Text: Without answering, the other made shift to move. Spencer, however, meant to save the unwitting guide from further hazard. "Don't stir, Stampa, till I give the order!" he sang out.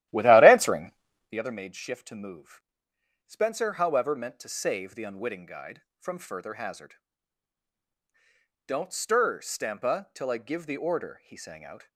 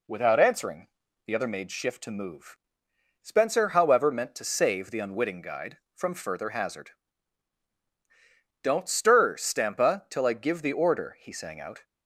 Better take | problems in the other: second | starts louder than the rest; strong; until 1.4 s; 13.5 dB

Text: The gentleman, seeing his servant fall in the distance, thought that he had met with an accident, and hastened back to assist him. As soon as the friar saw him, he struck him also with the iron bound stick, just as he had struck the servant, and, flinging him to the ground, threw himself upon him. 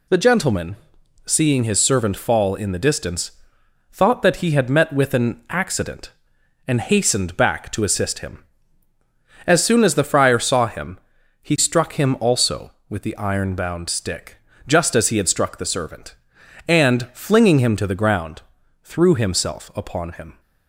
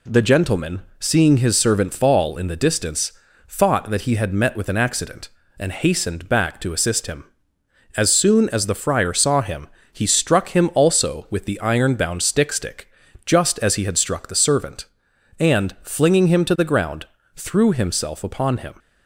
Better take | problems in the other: first | says "stick" twice; at 12.5 s

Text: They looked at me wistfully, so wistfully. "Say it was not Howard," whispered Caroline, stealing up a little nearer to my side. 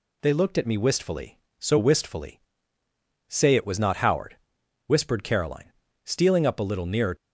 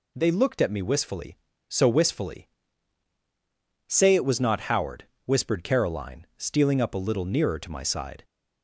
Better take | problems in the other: second | stops before "to my side"; at 7.1 s

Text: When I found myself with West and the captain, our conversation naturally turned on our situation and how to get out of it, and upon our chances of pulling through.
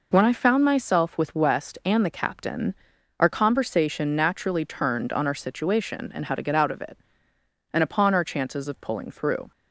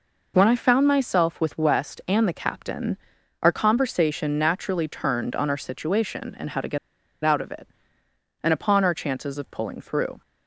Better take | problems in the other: first | pauses between "get" and "out"; noticeable; at 6.7 s; 0.47 s long

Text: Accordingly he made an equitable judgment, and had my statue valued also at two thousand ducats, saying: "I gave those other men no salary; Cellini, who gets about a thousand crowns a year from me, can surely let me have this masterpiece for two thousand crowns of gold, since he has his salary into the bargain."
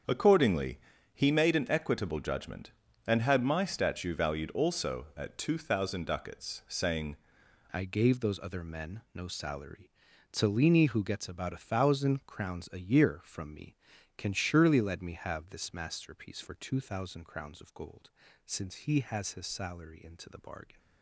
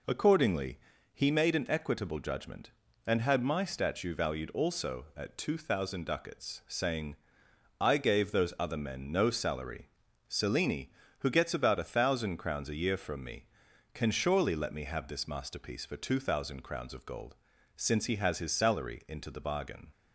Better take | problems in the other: second | starts louder than the rest; strong; until 1.4 s; 7 dB // pauses between "Accordingly" and "he"; slight; at 0.7 s; 0.36 s long; slight in the second // changes voice at "I"; from 7.7 s on; 13.0 s long

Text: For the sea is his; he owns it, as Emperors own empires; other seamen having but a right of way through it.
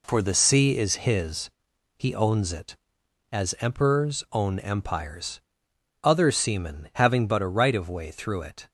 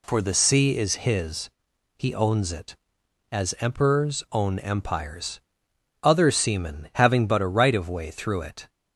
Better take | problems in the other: second | gets quieter; throughout; 7 dB

